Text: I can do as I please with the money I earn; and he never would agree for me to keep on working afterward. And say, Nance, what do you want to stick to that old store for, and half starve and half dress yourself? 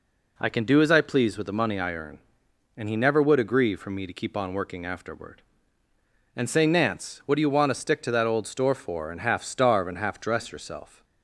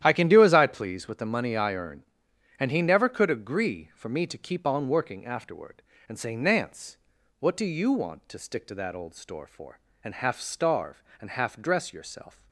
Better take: first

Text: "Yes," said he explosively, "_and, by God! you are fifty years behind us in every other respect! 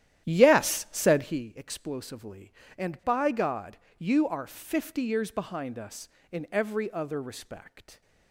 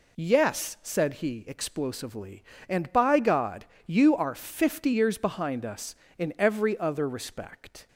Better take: second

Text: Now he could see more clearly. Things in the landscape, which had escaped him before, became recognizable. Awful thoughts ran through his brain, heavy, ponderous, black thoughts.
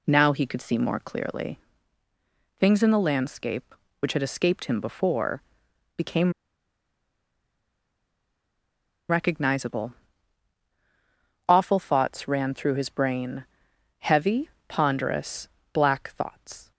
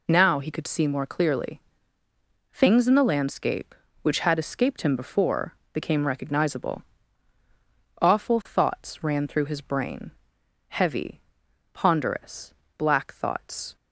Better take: second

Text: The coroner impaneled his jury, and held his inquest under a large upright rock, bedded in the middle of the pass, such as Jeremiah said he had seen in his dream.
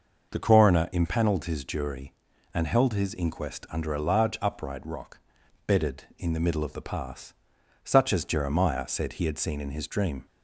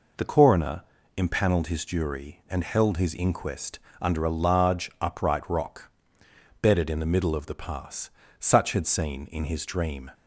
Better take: first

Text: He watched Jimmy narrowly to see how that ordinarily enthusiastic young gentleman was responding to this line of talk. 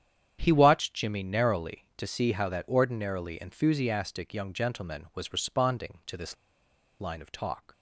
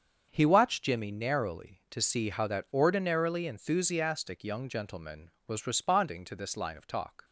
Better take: second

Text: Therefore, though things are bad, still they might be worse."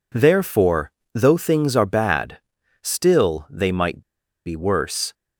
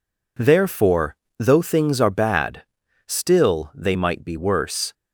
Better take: second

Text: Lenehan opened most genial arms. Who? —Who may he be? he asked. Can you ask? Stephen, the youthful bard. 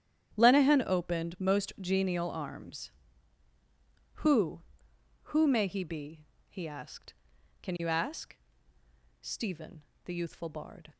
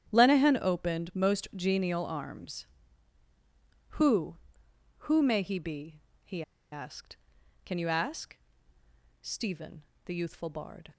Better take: first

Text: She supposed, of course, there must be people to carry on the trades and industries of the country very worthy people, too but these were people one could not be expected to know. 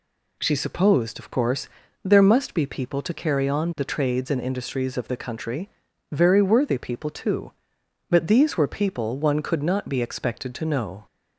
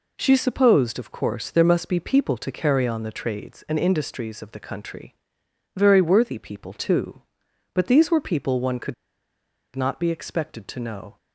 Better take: first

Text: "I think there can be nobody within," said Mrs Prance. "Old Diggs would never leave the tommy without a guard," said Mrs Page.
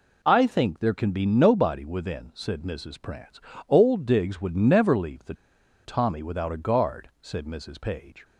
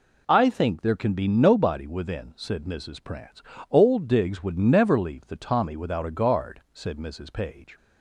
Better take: second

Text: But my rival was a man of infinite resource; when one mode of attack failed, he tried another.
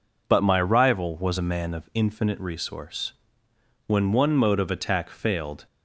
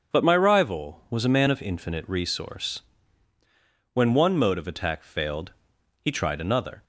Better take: second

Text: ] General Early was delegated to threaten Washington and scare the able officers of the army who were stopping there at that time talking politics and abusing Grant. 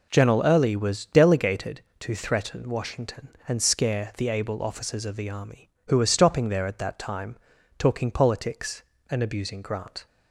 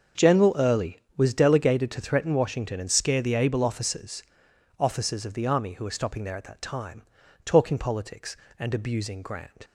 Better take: first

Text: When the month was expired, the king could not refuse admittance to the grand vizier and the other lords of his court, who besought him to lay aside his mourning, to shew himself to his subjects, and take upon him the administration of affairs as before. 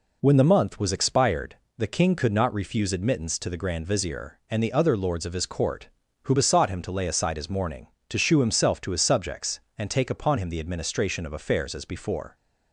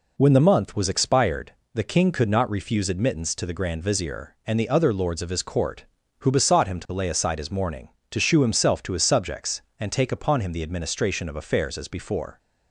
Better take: neither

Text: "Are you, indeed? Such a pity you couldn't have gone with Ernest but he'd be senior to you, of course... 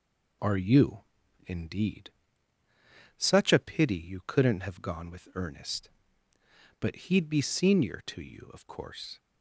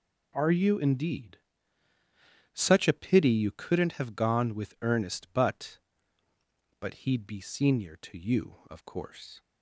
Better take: first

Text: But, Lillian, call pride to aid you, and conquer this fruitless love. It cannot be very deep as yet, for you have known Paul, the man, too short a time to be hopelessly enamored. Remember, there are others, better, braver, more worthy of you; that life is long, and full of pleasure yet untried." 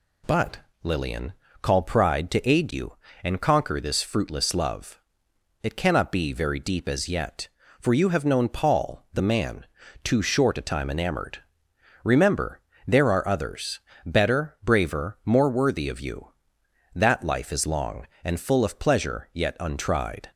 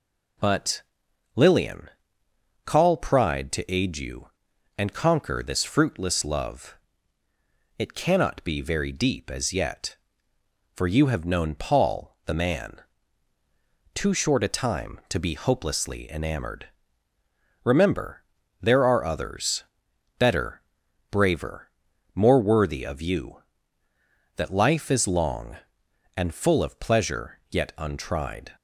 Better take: second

